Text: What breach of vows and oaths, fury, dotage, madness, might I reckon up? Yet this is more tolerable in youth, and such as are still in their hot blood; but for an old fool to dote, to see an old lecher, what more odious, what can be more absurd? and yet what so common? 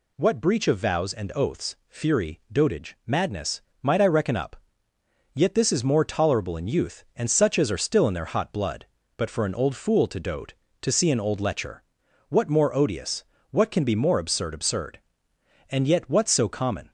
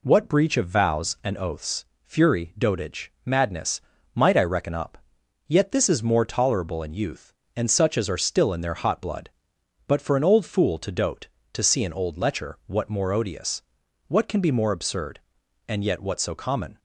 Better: second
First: says "absurd" twice; at 14.5 s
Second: none

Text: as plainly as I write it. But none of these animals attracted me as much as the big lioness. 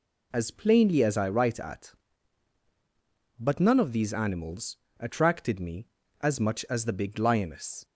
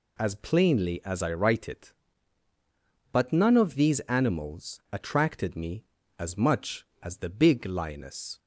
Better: second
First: says "at" for "it"; at 1.5 s // pauses between "animals" and "attracted"; slight; at 4.7 s; 0.22 s long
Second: none

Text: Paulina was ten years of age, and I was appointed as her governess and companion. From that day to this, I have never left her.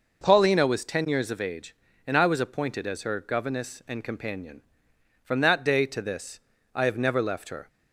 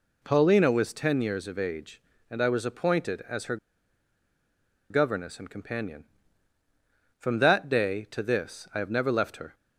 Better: first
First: none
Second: pauses between "her" and "governess"; strong; at 3.5 s; 1.3 s long

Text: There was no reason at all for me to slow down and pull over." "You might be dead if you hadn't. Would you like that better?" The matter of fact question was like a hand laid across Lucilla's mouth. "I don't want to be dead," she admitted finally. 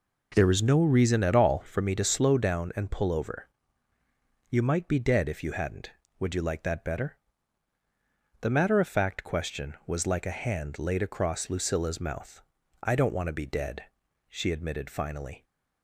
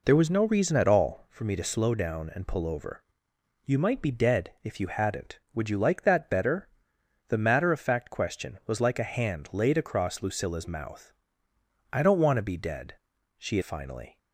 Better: first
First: none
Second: skips "admitted"; at 13.6 s

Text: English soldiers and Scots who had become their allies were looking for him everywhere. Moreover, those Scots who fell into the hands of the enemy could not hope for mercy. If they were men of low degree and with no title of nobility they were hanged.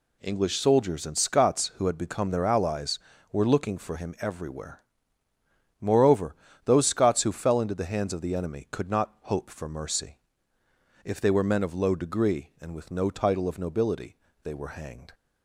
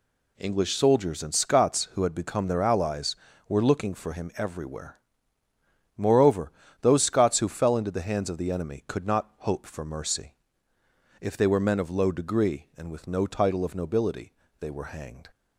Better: neither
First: pauses between "nobility" and "they"; slight; at 14.1 s; 0.26 s long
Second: pauses between "nobility" and "they"; slight; at 14.3 s; 0.26 s long

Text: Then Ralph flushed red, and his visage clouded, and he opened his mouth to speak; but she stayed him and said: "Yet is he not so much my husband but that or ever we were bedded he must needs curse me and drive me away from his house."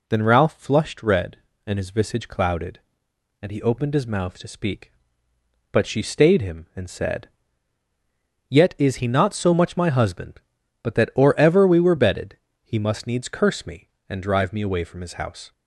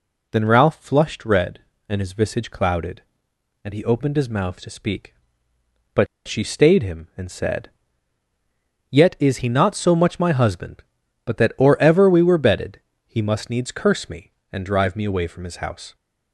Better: first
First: pauses between "bedded" and "he"; slight; at 12.3 s; 0.28 s long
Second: pauses between "but" and "she"; slight; at 6.0 s; 0.19 s long // pauses between "bedded" and "he"; slight; at 12.7 s; 0.28 s long

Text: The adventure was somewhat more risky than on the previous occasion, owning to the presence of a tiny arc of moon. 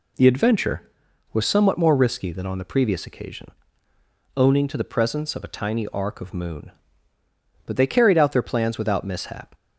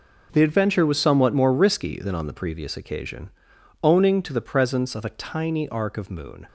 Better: second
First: goes on to say "But they carried out their plans without mishap"; strong; from 7.6 s on; 1.9 s long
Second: none

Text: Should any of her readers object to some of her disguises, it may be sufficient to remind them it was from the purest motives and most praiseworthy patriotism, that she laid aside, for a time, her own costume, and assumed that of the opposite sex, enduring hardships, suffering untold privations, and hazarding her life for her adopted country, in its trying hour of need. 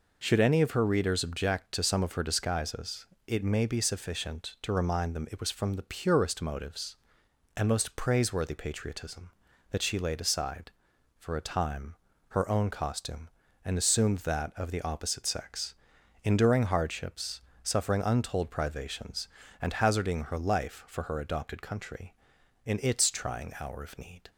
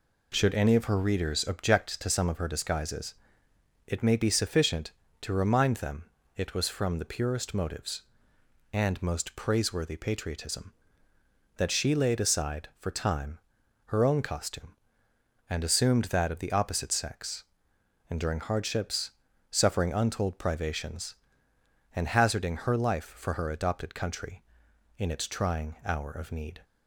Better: first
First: none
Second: pauses between "them" and "it"; slight; at 6.0 s; 0.30 s long // skips "a"; at 12.8 s

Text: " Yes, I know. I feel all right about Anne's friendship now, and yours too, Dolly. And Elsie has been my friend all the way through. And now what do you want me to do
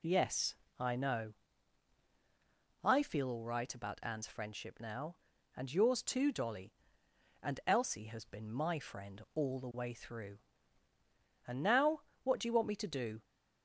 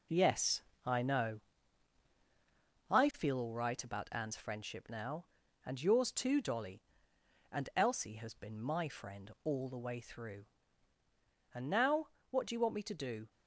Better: first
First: pauses between "now" and "what"; slight; at 12.0 s; 0.20 s long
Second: gets quieter; strong; throughout; 7.5 dB // pauses between "now" and "what"; slight; at 12.0 s; 0.20 s long

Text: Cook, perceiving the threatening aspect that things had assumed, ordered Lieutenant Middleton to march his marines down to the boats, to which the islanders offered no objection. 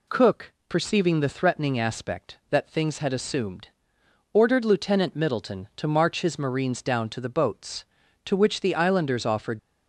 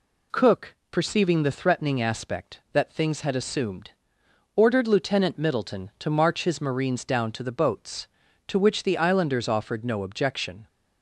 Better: second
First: stops before "no objection"; at 9.5 s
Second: none

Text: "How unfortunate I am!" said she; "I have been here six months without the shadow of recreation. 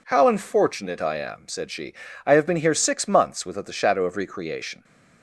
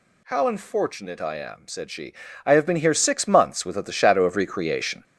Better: first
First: none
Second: gets louder; noticeable; throughout; 6 dB

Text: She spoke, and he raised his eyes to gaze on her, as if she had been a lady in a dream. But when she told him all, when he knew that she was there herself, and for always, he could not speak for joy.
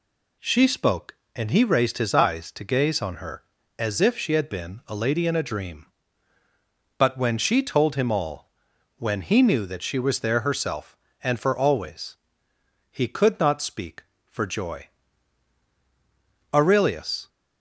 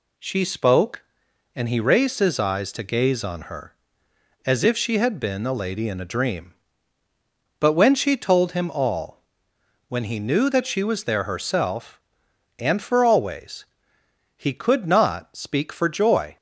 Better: second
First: goes on to say "Aurelius"; noticeable; from 16.5 s on; 0.76 s long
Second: none

